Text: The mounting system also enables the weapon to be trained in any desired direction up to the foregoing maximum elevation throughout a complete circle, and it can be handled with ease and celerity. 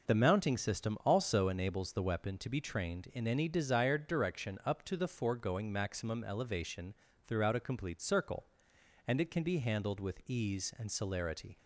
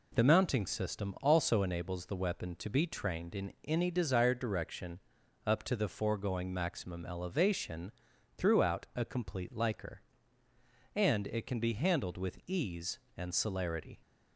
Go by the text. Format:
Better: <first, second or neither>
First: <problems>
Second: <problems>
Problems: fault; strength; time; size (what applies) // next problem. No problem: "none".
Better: first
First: pauses between "elevation" and "throughout"; slight; at 6.9 s; 0.32 s long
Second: pauses between "in" and "any"; slight; at 3.5 s; 0.16 s long // pauses between "direction" and "up"; noticeable; at 4.9 s; 0.46 s long // pauses between "elevation" and "throughout"; noticeable; at 7.9 s; 0.46 s long // says "liker" for "circle"; at 9.5 s